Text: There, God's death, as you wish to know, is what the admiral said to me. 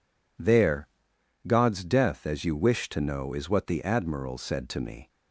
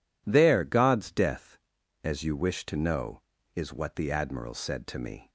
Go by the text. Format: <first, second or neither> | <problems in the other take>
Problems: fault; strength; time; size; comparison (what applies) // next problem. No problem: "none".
neither | none